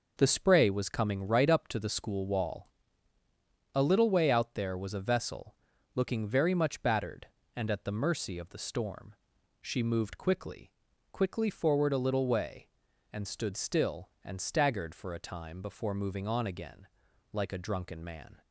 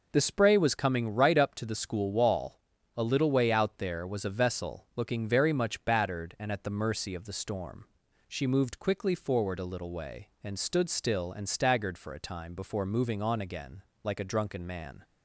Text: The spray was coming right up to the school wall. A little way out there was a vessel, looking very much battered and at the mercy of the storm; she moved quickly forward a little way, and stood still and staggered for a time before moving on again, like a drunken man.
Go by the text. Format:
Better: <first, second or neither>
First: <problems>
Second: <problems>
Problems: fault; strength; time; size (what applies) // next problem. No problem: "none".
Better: second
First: says "quickly" twice; at 11.1 s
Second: none